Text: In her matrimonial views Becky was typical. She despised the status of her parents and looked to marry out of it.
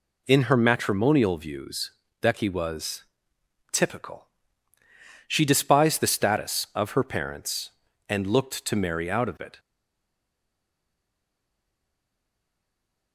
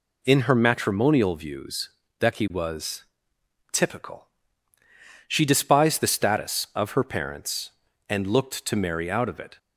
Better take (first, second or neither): second